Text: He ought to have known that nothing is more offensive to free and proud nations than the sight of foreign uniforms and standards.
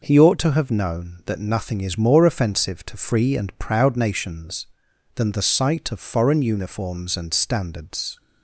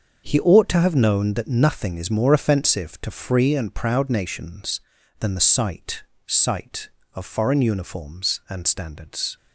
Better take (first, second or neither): first